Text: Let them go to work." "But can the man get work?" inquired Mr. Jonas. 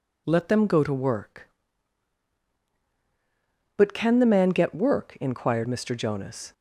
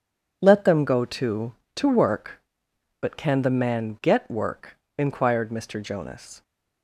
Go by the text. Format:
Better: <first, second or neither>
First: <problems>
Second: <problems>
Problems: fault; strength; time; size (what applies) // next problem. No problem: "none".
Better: first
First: none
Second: says "to" twice; at 1.7 s